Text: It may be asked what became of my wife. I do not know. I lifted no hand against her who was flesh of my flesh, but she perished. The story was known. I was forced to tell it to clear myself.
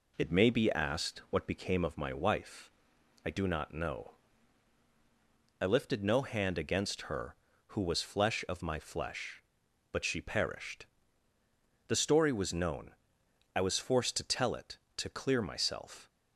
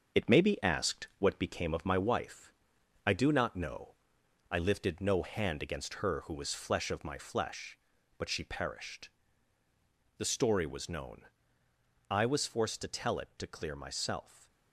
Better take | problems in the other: first | gets quieter; noticeable; throughout; 4.5 dB

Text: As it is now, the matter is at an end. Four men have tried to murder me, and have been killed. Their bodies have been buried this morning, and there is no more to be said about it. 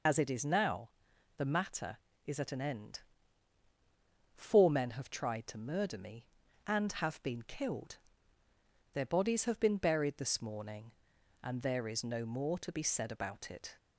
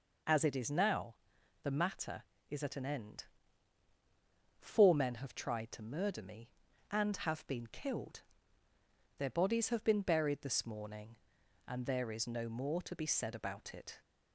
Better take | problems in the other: second | loses the start of "As"; at 0.0 s; 55 ms

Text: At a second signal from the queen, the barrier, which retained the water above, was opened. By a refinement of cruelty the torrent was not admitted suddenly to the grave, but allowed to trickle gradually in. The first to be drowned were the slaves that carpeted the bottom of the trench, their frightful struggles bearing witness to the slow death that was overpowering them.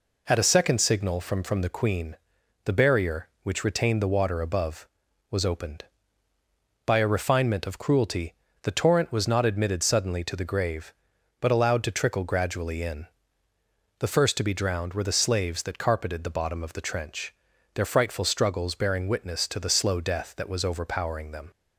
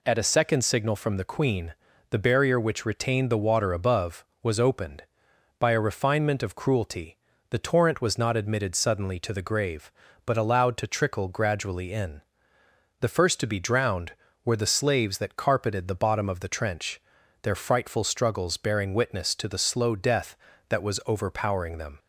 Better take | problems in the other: second | says "from" twice; at 1.4 s // pauses between "cruelty" and "the"; slight; at 8.3 s; 0.28 s long; slight in the second

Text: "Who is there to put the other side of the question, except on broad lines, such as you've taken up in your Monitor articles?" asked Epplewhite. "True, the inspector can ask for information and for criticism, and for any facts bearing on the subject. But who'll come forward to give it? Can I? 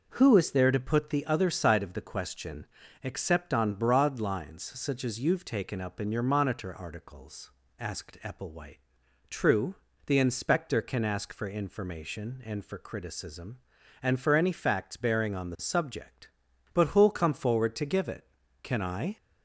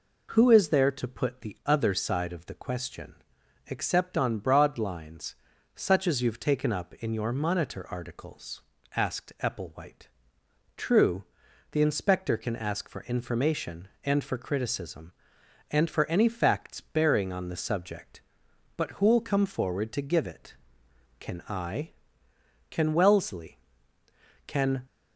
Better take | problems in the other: first | goes on to say "Can Wellesley Can"; strong; from 22.6 s on; 2.1 s long

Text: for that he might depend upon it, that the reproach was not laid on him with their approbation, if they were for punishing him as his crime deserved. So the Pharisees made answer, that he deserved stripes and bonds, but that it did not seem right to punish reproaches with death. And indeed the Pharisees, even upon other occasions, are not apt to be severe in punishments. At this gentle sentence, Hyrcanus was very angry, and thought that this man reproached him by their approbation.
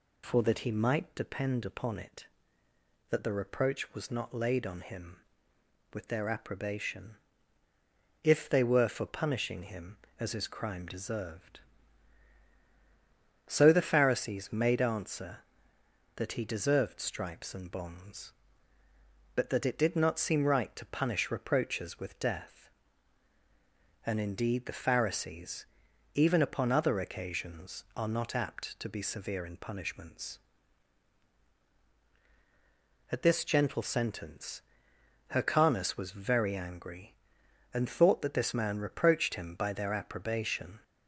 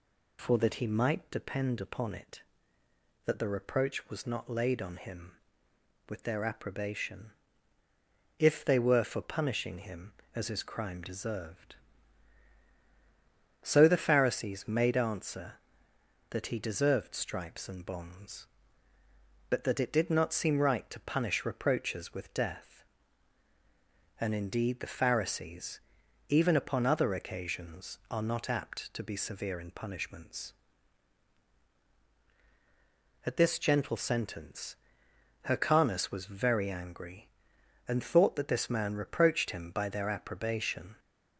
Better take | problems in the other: neither | none

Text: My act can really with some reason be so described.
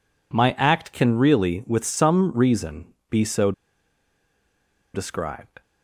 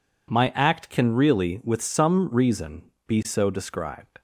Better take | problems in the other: second | pauses between "reason" and "be"; slight; at 2.9 s; 0.16 s long; slight in the second // pauses between "so" and "described"; strong; at 3.5 s; 1.4 s long

